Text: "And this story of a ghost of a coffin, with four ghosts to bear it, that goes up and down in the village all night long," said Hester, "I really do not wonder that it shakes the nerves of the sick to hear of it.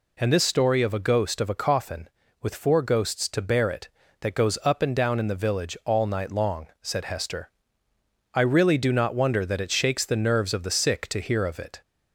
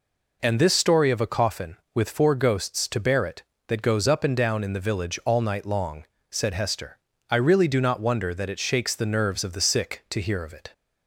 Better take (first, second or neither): first